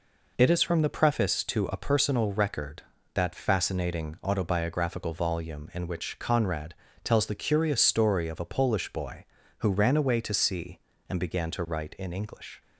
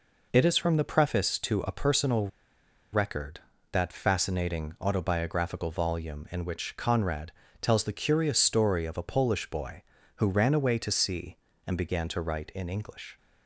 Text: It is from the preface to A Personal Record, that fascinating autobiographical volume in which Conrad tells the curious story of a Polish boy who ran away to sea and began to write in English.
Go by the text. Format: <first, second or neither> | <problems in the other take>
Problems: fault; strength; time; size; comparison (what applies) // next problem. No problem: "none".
first | pauses between "Personal" and "Record"; noticeable; at 2.2 s; 0.64 s long // pauses between "Conrad" and "tells"; slight; at 7.3 s; 0.30 s long; slight in the first